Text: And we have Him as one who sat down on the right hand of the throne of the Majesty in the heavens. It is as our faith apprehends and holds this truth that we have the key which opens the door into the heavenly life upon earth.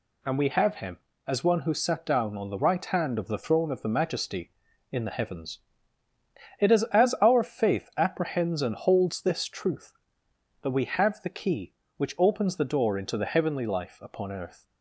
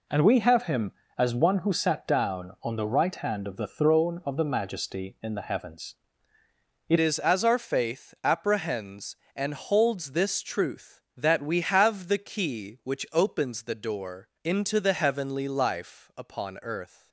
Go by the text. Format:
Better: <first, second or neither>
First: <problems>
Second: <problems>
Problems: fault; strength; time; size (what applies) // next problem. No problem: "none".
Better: first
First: none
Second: changes voice at "is"; from 6.9 s on; 10.1 s long // pauses between "door" and "into"; slight; at 14.2 s; 0.16 s long